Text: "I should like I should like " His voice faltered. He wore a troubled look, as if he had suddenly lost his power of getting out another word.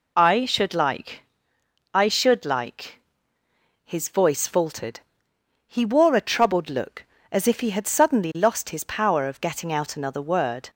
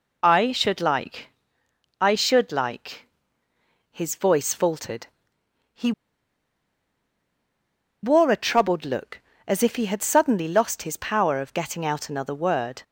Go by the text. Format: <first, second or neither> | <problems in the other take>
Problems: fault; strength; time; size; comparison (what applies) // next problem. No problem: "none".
first | pauses between "like" and "I"; noticeable; at 1.2 s; 0.72 s long; noticeable in the first // pauses between "He" and "wore"; strong; at 5.9 s; 2.1 s long